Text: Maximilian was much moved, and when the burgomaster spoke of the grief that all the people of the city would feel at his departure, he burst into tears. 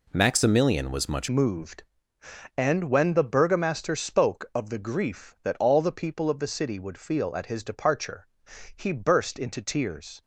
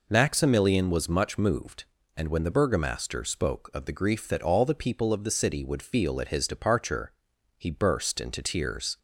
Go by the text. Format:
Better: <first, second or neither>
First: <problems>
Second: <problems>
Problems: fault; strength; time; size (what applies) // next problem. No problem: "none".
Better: second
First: changes voice at "moved"; from 1.2 s on; 9.0 s long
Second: none